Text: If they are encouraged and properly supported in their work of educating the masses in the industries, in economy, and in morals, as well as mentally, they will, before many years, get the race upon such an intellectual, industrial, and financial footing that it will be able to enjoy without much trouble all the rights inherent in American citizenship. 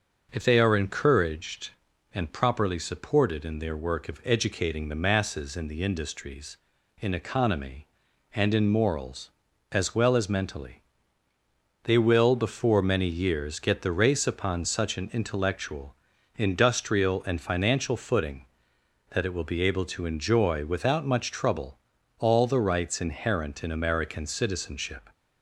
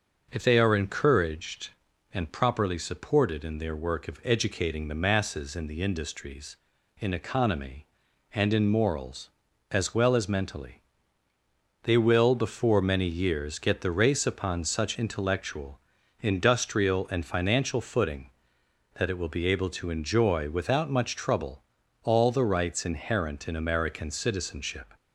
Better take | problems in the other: first | skips "an"; at 14.9 s // pauses between "trouble" and "all"; at 21.6 s; 0.40 s long; also in the first

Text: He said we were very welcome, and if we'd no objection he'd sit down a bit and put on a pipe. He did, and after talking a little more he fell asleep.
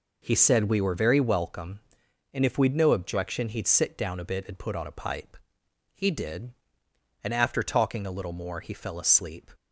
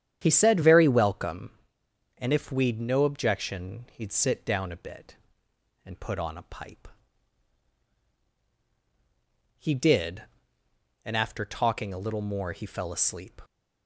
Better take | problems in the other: first | starts louder than the rest; strong; until 1.2 s; 9.5 dB // skips "we were"; at 0.6 s

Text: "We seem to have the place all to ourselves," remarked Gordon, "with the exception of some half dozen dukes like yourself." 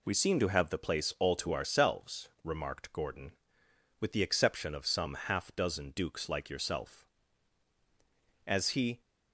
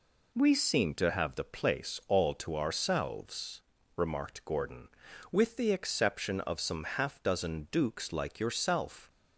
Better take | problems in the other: second | goes on to say "As he"; from 8.4 s on; 0.54 s long

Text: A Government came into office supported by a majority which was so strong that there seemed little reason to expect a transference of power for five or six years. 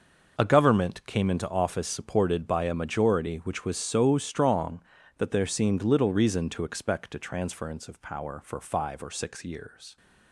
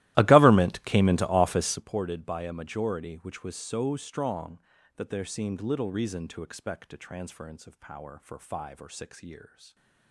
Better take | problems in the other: first | starts louder than the rest; strong; until 1.9 s; 16.5 dB // stays silent after the last word; slight; from 9.4 s on; 0.7 s long

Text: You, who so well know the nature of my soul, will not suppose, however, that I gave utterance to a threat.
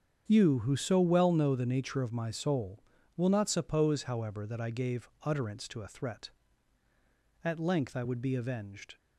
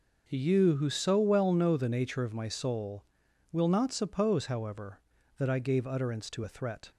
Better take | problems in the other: second | starts louder than the rest; strong; until 1.2 s; 7.5 dB // goes on to say "At length I would be avenged"; from 7.4 s on; 1.5 s long

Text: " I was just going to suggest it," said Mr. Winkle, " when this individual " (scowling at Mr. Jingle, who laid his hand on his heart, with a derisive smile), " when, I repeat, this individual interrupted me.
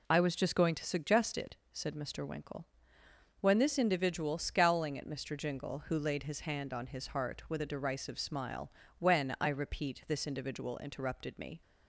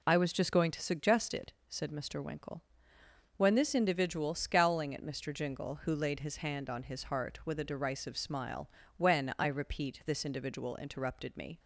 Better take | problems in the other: neither | none

